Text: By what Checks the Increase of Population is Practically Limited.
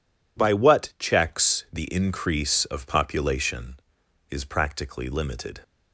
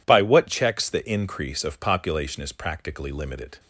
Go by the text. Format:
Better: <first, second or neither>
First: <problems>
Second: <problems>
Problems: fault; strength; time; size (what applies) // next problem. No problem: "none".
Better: neither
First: none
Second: none